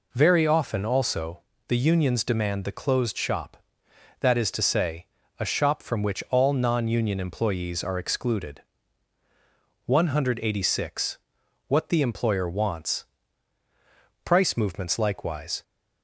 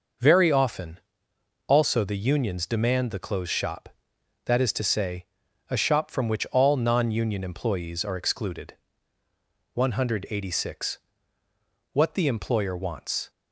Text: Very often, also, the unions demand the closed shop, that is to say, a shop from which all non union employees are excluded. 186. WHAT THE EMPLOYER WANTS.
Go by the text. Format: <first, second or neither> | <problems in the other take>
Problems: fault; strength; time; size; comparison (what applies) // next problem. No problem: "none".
second | goes on to say "Price movements likewise"; from 14.2 s on; 1.3 s long